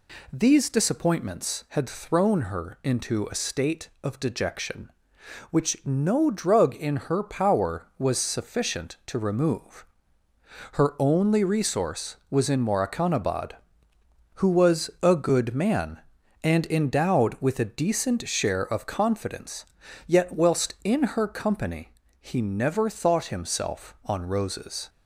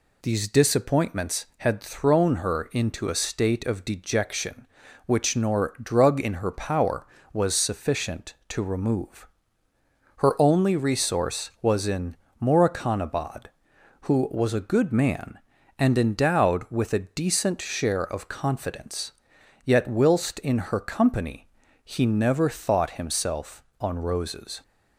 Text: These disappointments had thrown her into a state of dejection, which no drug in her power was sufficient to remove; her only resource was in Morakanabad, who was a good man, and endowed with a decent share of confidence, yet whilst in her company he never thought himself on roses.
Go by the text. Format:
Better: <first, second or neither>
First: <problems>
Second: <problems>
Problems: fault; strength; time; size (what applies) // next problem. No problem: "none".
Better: first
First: pauses between "company" and "he"; slight; at 21.9 s; 0.26 s long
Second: says "nor" for "no"; at 5.3 s // pauses between "in" and "Morakanabad"; slight; at 12.1 s; 0.24 s long // pauses between "company" and "he"; at 21.4 s; 0.38 s long